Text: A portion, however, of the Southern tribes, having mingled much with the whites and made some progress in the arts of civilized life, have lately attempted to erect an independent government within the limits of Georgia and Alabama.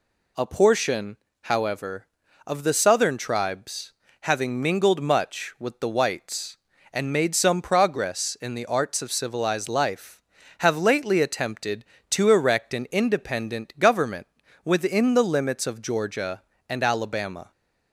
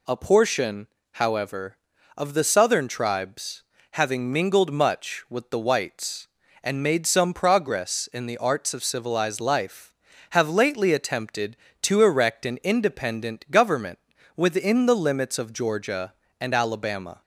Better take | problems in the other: neither | pauses between "government" and "within"; slight; the same in both

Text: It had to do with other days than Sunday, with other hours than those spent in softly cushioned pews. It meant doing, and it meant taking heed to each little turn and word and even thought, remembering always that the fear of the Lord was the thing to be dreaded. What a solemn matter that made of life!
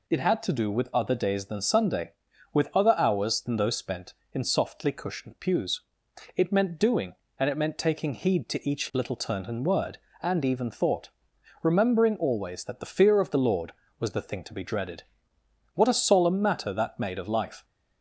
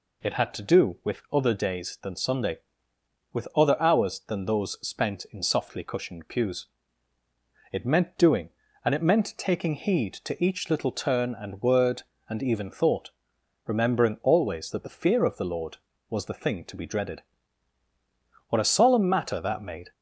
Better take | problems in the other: first | stops before "of life"; at 19.9 s

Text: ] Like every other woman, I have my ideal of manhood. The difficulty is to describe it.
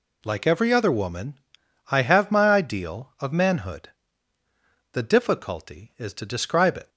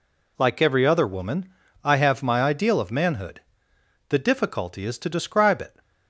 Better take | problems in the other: neither | none

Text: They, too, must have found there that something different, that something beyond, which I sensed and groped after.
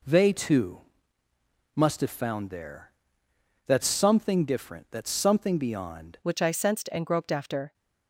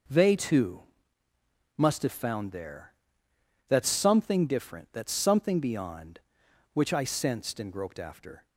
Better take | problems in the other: second | changes voice at "which"; from 6.2 s on; 1.5 s long

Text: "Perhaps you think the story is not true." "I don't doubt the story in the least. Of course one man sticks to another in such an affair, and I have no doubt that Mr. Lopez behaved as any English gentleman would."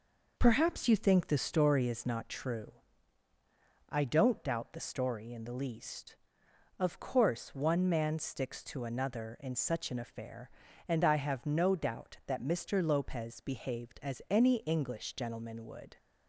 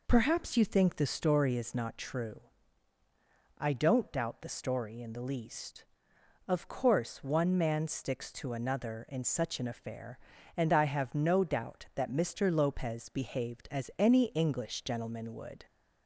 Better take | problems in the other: second | gets quieter; noticeable; throughout; 4.5 dB

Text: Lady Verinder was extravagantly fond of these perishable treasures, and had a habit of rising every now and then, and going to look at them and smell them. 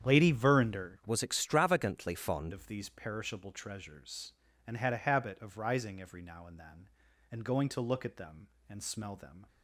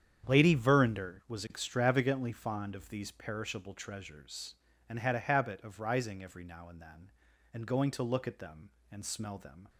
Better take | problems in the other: second | starts louder than the rest; strong; until 1.1 s; 8.5 dB; strong in the second // changes voice from "was" to "fond"; from 1.0 to 2.5 s; 1.5 s long

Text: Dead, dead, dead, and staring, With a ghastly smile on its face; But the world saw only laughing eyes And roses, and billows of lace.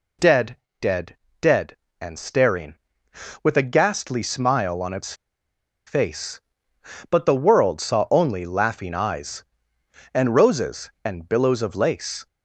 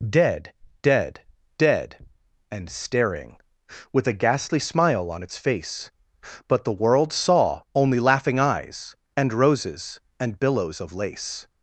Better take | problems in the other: second | pauses between "its" and "face"; noticeable; at 5.1 s; 0.72 s long

